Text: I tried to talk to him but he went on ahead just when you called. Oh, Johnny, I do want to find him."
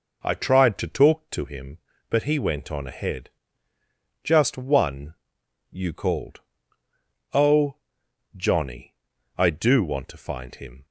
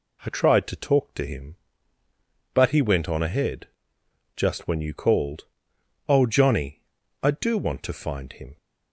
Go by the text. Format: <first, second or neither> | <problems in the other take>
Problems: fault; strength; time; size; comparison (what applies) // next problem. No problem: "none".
second | pauses between "ahead" and "just"; noticeable; at 3.2 s; 0.92 s long; noticeable in the second // says "one" for "when"; at 4.5 s